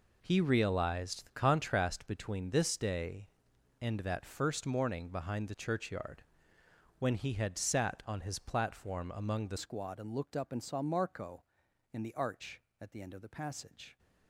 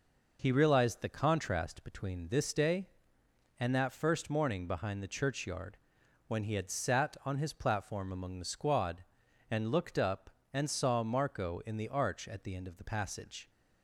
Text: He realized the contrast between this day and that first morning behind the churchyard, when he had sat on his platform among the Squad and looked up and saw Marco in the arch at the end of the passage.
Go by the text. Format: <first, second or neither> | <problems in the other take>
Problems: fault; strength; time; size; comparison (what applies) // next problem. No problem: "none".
second | changes voice at "Squad"; from 9.5 s on; 4.4 s long